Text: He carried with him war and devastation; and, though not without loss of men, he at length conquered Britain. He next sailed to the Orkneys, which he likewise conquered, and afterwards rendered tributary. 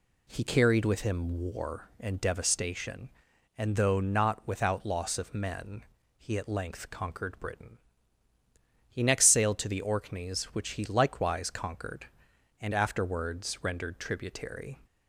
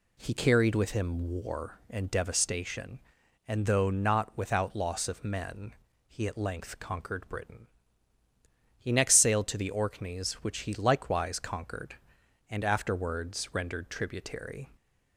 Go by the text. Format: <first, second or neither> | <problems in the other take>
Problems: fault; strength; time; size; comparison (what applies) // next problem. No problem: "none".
neither | none